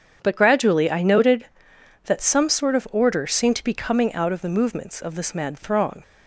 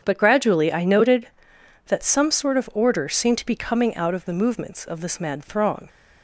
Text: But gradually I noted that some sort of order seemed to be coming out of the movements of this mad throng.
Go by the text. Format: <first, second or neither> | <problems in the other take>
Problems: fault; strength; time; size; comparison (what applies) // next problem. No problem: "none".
neither | starts louder than the rest; strong; the same in both